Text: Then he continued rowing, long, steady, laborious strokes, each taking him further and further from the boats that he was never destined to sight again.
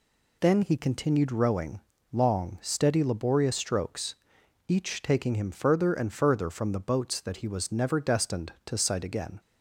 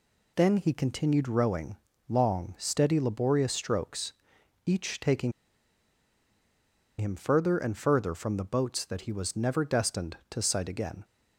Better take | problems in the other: first | pauses between "taking" and "him"; strong; at 5.3 s; 1.6 s long

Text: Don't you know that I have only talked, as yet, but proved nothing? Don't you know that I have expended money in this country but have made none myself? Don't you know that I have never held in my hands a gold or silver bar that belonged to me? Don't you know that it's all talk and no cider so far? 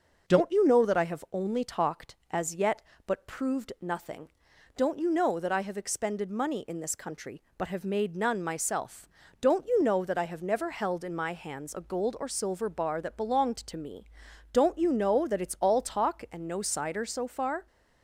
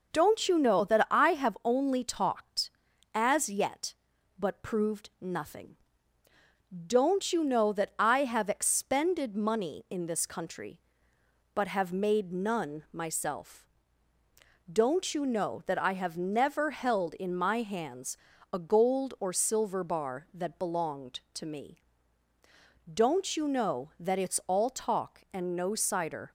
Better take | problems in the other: first | pauses between "hands" and "a"; at 18.1 s; 0.38 s long // stops before "so far"; at 26.2 s

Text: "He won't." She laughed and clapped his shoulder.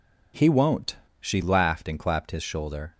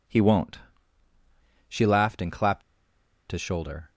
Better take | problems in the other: first | pauses between "clapped" and "his"; noticeable; at 2.6 s; 0.68 s long

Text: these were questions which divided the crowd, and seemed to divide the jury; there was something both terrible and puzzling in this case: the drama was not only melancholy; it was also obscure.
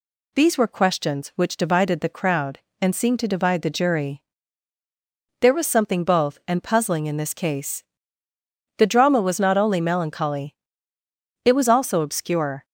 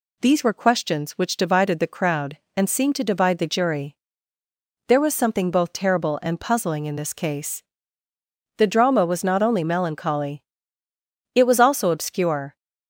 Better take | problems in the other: second | skips "terrible"; at 6.4 s

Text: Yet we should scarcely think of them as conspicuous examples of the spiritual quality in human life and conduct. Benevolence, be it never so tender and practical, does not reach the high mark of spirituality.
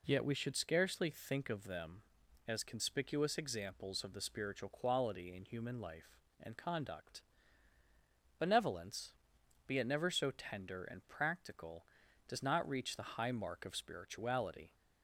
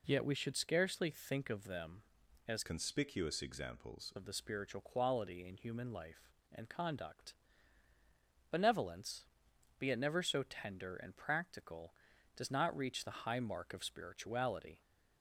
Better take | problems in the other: first | changes voice from "conspicuous" to "examples"; from 2.6 to 4.1 s; 1.5 s long

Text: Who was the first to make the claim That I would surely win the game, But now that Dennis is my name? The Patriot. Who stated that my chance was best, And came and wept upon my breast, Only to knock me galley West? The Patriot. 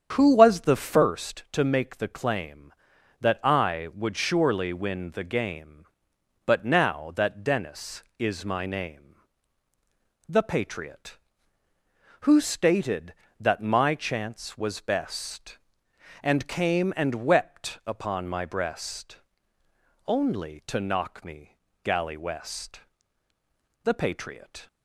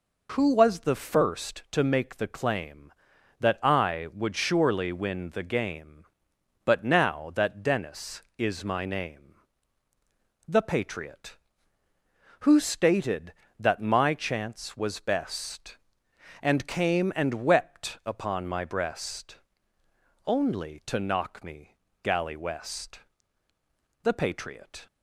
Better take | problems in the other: second | starts louder than the rest; strong; until 1.2 s; 8 dB // pauses between "me" and "galley"; slight; at 21.5 s; 0.30 s long; slight in the second

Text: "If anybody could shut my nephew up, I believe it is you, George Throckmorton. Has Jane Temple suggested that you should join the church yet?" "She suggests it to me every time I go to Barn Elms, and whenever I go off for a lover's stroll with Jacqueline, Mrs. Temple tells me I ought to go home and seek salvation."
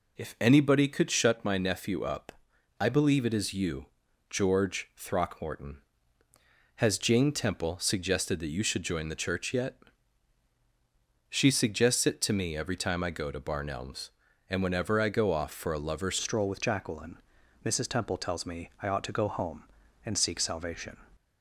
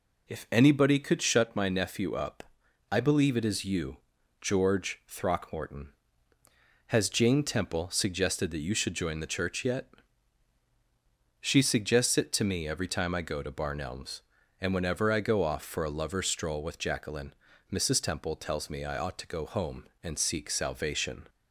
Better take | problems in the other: second | changes voice at "stroll"; from 16.2 s on; 4.7 s long

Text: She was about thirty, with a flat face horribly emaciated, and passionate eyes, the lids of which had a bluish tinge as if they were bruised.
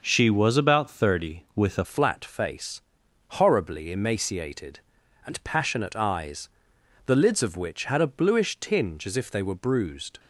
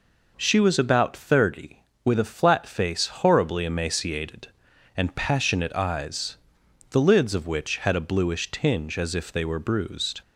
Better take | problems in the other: second | changes voice at "flat"; from 1.8 s on; 8.3 s long // pauses between "face" and "horribly"; noticeable; at 2.8 s; 0.50 s long

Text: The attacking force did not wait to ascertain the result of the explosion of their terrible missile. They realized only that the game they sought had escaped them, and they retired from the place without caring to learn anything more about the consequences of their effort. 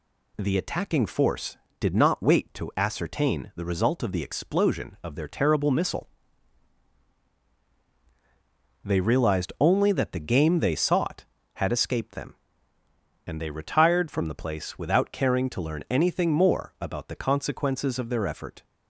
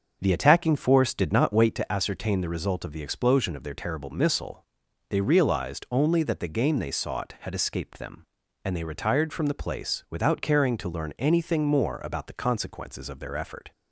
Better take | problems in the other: first | starts louder than the rest; until 1.9 s; 6.5 dB

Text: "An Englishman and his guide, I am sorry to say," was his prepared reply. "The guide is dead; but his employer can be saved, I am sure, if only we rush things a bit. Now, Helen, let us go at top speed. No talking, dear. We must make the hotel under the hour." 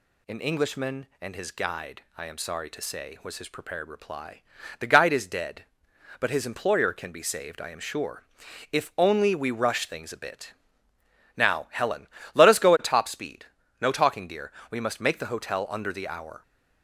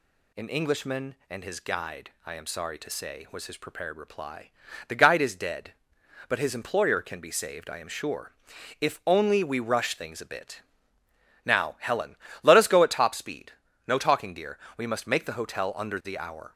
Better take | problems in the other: neither | none

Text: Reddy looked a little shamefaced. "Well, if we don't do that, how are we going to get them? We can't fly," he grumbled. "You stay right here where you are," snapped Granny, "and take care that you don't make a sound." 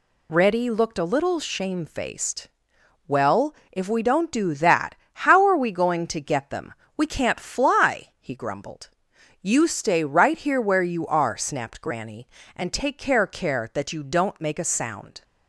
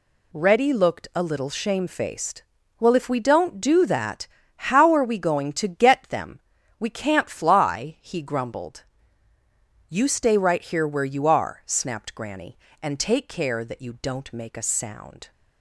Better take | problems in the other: second | says "care" twice; at 13.2 s

